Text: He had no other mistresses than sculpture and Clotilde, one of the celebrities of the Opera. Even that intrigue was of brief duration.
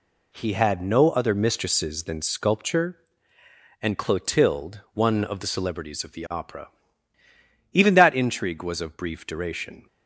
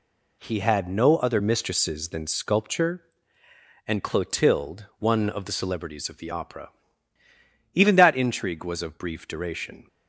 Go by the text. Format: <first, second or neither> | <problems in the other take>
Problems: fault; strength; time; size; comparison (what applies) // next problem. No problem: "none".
neither | none